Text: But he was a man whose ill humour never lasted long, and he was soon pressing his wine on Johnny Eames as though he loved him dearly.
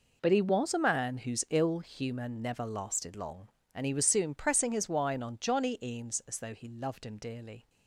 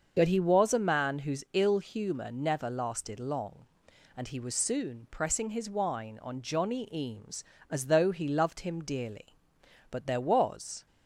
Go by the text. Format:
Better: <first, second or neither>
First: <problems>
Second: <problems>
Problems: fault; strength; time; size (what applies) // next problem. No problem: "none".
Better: first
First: none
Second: starts louder than the rest; until 1.1 s; 6.5 dB // goes on to say "But there was"; noticeable; from 9.9 s on; 0.94 s long